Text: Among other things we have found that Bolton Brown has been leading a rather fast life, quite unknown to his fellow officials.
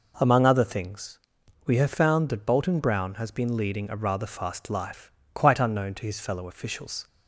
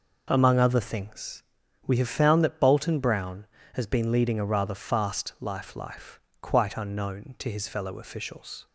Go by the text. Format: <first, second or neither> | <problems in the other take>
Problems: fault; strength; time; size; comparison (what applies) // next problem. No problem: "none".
first | pauses between "things" and "we"; at 1.4 s; 0.43 s long; noticeable in the first // says "life" twice; at 5.7 s